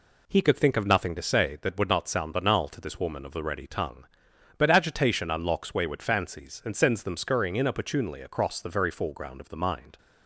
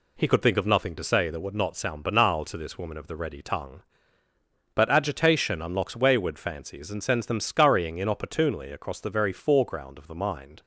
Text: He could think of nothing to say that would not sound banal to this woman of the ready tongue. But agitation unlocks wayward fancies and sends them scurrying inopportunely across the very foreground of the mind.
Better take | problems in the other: neither | none

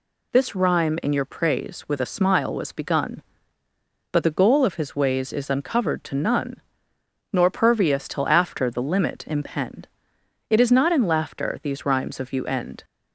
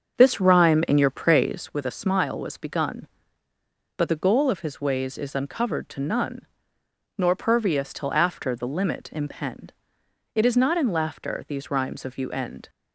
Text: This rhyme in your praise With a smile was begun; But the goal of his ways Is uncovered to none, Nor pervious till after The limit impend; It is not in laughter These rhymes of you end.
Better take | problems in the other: first | starts louder than the rest; until 1.7 s; 7 dB

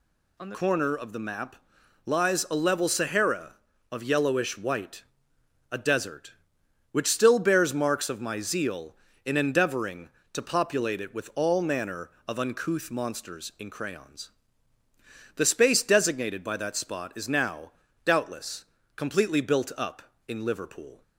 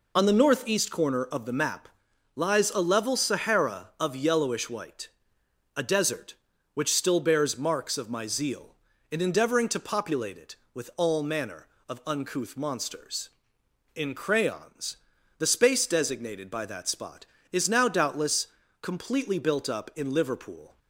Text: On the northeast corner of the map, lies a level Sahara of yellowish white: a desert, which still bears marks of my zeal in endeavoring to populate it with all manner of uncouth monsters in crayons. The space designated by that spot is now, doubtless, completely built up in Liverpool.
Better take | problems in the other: second | skips "northeast"; at 0.5 s

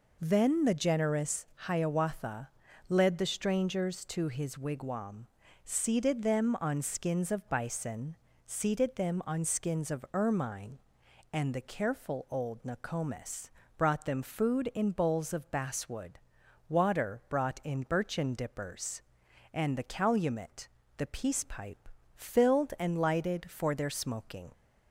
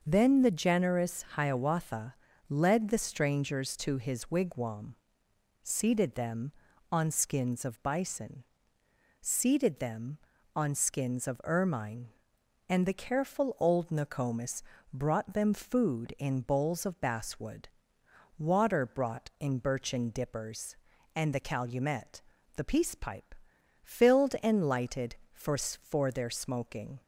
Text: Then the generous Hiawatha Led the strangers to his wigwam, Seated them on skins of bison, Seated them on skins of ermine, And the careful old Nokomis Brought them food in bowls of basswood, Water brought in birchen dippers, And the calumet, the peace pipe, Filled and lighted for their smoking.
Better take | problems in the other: first | pauses between "Hiawatha" and "Led"; slight; at 2.1 s; 0.34 s long; also in the first // pauses between "Nokomis" and "Brought"; slight; at 14.6 s; 0.32 s long; slight in the first // says "for" twice; at 25.5 s

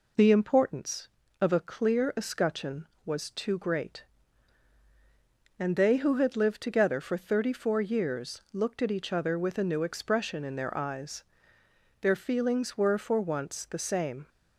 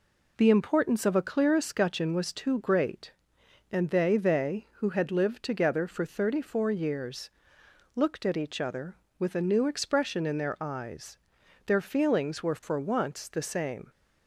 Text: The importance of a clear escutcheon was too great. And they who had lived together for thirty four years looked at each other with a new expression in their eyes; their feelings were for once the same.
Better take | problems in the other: first | says "they" twice; at 4.1 s // pauses between "years" and "looked"; noticeable; at 7.3 s; 0.64 s long

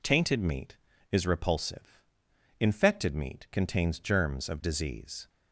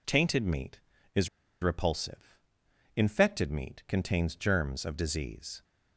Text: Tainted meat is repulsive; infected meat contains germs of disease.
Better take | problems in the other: first | pauses between "is" and "repulsive"; slight; at 1.2 s; 0.34 s long

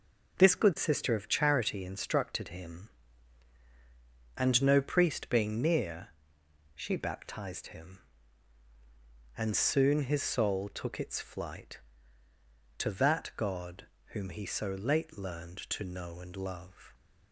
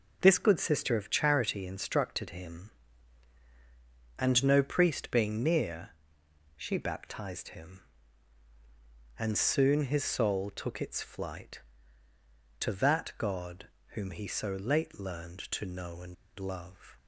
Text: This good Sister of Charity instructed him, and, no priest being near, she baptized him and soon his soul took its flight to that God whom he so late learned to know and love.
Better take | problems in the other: first | pauses between "God" and "whom"; slight; at 13.6 s; 0.26 s long; slight in the first // pauses between "and" and "love"; slight; at 16.1 s; 0.24 s long

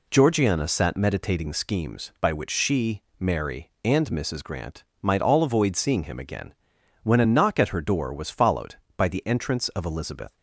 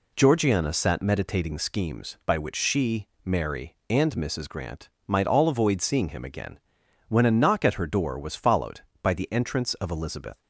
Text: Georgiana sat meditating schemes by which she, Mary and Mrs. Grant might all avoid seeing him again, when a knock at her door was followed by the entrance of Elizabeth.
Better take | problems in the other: neither | pauses between "Grant" and "might"; slight; the same in both

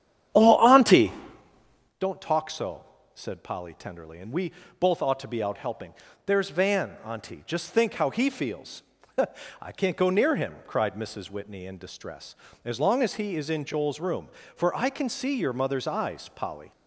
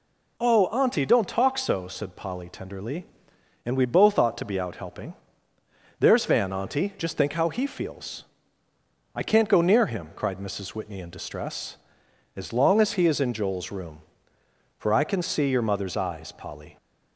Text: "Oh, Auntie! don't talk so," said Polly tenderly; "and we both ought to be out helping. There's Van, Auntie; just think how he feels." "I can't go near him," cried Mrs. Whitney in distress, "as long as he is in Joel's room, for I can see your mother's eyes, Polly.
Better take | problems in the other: second | starts louder than the rest; strong; until 2.0 s; 8.5 dB // pauses between "we" and "both"; slight; at 4.5 s; 0.28 s long

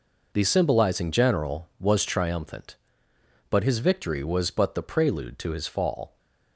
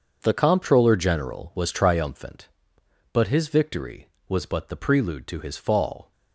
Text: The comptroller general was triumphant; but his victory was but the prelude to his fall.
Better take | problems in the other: second | says "symbolizing" for "comptroller"; at 0.4 s

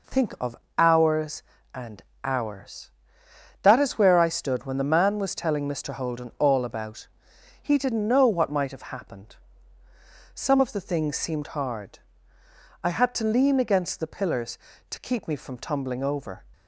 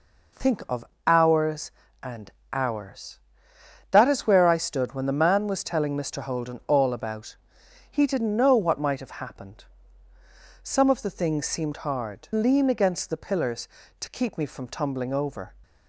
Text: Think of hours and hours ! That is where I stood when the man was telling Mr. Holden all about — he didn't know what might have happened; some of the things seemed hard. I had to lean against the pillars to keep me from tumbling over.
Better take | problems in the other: first | pauses between "of" and "hours"; slight; at 0.8 s; 0.22 s long; slight in the first // pauses between "and" and "hours"; slight; at 2.3 s; 0.20 s long; slight in the first // skips "I had to"; at 12.3 s

